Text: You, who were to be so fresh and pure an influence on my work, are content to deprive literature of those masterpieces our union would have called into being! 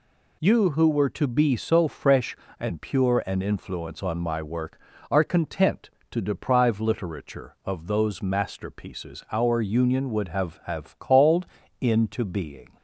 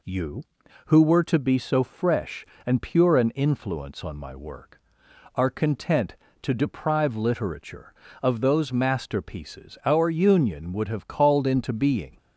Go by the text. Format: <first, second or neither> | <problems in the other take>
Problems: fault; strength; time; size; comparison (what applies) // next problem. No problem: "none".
second | says "have" twice; at 10.6 s // pauses between "called" and "into"; slight; at 11.4 s; 0.34 s long